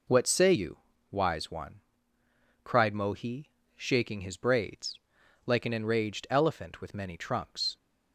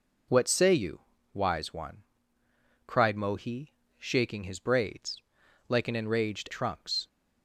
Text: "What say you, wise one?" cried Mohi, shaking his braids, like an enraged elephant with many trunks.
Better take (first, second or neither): first